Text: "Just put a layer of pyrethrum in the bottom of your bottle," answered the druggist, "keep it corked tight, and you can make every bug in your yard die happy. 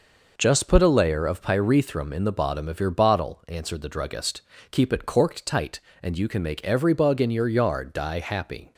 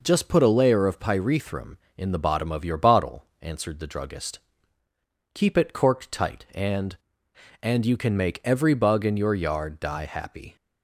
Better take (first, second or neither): first